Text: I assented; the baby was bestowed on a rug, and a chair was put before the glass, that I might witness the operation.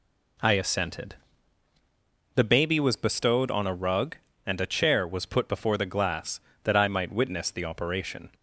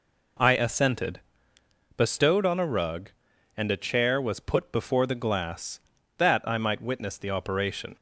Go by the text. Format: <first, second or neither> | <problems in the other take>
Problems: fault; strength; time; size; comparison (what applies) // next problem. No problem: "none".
first | skips "the baby was"; at 1.5 s